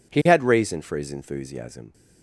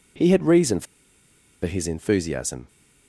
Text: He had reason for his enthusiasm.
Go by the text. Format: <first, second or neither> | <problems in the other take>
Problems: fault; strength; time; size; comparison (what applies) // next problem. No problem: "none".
first | pauses between "for" and "his"; noticeable; at 0.8 s; 0.79 s long